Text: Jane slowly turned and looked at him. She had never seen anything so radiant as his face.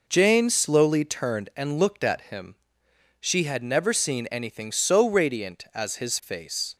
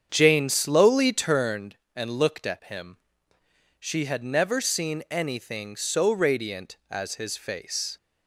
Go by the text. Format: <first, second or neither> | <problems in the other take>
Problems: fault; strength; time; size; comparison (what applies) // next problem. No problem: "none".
first | starts louder than the rest; strong; until 1.7 s; 7.5 dB